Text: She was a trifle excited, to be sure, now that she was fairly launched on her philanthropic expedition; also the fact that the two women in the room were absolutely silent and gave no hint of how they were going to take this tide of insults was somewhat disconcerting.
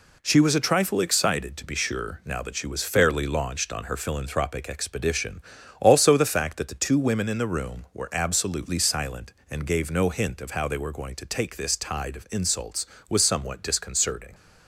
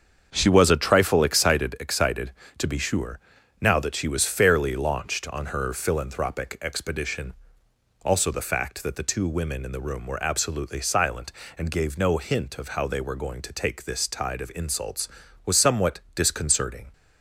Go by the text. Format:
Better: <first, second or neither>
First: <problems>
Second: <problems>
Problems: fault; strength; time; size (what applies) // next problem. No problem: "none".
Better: first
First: none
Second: starts louder than the rest; until 1.3 s; 7 dB // says "excited" twice; at 1.8 s // pauses between "somewhat" and "disconcerting"; slight; at 15.9 s; 0.16 s long